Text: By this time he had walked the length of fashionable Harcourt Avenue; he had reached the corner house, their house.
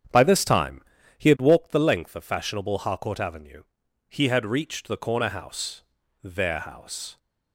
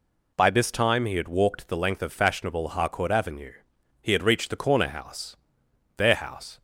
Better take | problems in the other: second | starts louder than the rest; strong; until 1.7 s; 9 dB // pauses between "time" and "he"; slight; at 0.8 s; 0.36 s long

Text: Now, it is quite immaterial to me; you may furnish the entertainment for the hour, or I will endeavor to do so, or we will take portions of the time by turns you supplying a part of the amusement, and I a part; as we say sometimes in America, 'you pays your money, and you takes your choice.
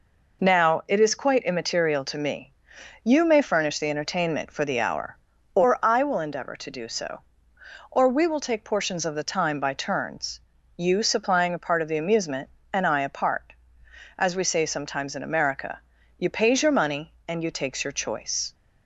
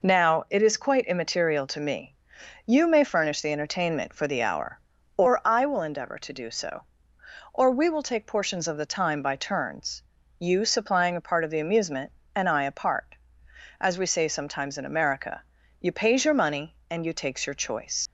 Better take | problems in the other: first | pauses between "turns" and "you"; at 10.0 s; 0.38 s long; also in the first // leaves "choice" unfinished; at 18.0 s; 110 ms

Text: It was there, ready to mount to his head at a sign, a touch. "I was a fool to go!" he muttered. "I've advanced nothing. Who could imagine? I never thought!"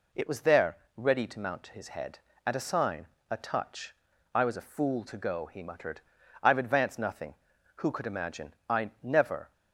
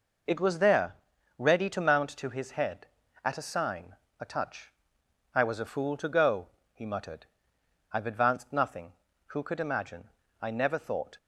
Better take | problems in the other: second | stops before "thought"; at 9.5 s

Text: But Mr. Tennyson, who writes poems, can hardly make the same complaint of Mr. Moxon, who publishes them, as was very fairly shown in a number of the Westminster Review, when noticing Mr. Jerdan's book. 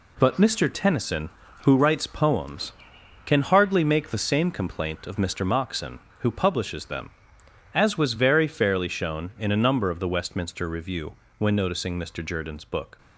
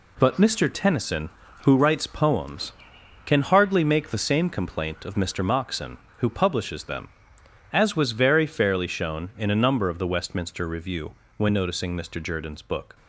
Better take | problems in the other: neither | none

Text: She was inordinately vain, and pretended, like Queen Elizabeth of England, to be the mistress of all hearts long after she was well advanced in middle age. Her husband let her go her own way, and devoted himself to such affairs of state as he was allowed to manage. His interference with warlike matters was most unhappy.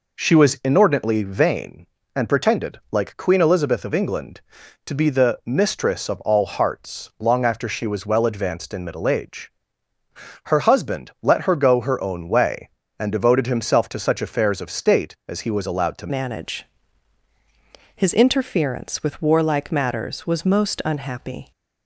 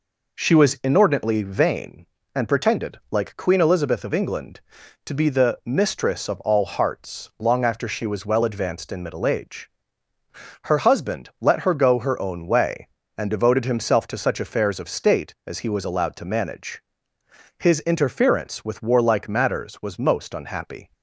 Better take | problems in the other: second | changes voice at "manage"; from 16.0 s on; 5.5 s long

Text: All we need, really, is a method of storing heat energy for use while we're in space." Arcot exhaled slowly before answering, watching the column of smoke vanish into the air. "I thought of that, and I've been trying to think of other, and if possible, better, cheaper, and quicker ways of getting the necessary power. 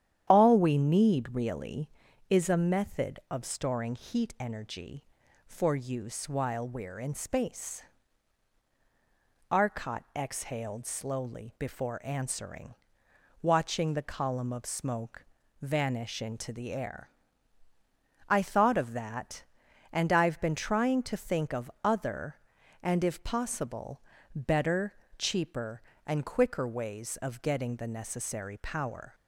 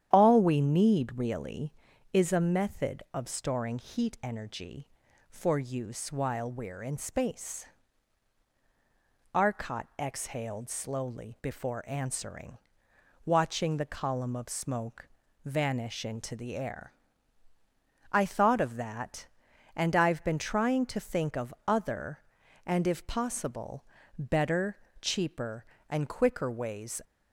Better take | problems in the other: first | starts louder than the rest; strong; until 1.1 s; 9.5 dB; strong in the first // pauses between "smoke" and "vanish"; at 15.0 s; 0.38 s long; also in the first // stops before "of getting the necessary power"; at 27.0 s

